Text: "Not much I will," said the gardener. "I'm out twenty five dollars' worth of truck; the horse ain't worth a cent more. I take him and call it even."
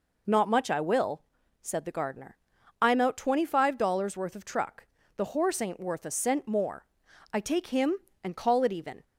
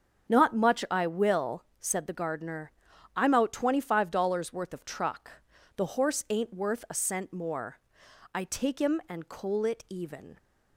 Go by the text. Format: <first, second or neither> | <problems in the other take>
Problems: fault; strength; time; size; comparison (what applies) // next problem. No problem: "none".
first | starts louder than the rest; strong; until 1.3 s; 8 dB // says "coal" for "call"; at 9.2 s